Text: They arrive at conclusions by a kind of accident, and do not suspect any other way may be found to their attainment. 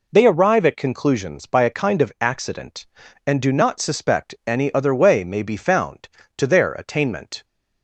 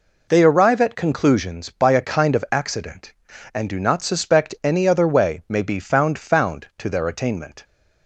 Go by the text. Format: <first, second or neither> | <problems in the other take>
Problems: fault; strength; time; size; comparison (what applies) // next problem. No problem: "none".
first | says "found" twice; at 6.1 s